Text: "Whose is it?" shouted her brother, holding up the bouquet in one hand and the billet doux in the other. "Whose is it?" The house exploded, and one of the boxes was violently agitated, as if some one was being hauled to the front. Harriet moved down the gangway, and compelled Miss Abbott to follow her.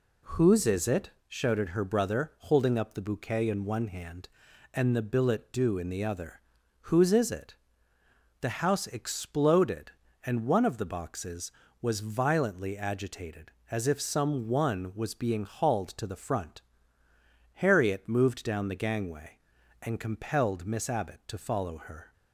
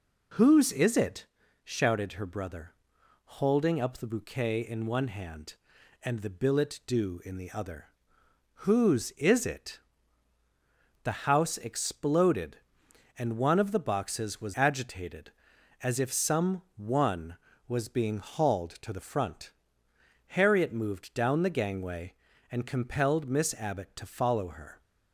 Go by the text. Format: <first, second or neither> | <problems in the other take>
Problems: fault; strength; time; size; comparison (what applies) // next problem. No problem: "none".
first | skips "violently"; at 14.5 s